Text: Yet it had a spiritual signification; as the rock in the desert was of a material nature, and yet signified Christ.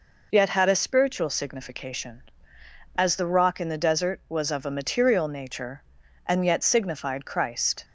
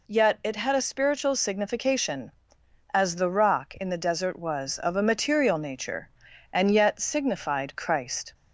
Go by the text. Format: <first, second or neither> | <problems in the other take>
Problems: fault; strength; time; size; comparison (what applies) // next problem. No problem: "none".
second | skips "it"; at 0.5 s